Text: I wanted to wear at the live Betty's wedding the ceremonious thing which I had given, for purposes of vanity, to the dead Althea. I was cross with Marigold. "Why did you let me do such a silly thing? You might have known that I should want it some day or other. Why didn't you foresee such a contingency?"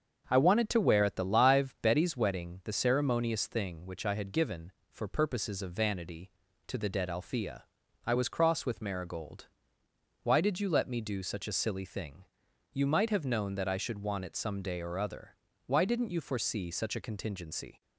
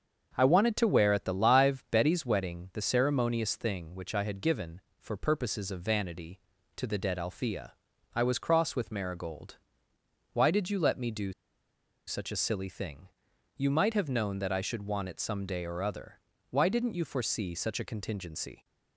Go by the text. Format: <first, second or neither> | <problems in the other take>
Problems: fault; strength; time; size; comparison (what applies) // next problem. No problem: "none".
first | starts louder than the rest; until 1.3 s; 7 dB; also in the first // pauses between "do" and "such"; noticeable; at 11.3 s; 0.74 s long